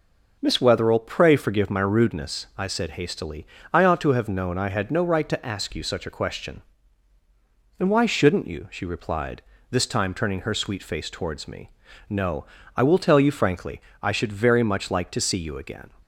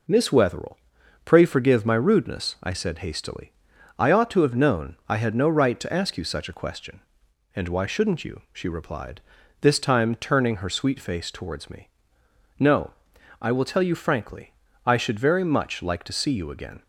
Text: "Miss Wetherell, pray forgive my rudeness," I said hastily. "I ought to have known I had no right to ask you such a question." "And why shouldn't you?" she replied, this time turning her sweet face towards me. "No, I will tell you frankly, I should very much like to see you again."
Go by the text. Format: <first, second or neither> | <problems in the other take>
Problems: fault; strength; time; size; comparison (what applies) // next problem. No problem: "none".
neither | none